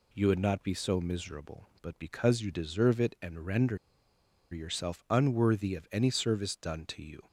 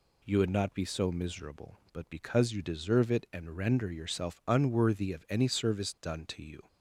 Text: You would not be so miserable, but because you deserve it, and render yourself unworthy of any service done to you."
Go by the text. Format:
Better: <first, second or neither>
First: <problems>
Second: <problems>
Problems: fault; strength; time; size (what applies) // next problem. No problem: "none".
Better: second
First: pauses between "render" and "yourself"; noticeable; at 3.7 s; 0.74 s long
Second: none